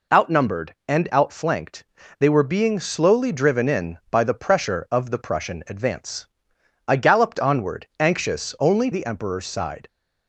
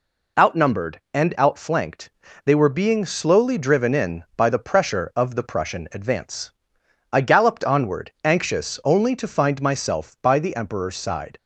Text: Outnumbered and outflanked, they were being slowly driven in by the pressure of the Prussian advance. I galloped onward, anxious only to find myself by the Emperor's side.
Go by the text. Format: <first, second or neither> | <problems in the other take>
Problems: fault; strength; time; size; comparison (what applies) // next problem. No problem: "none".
second | skips "to find myself by"; at 8.9 s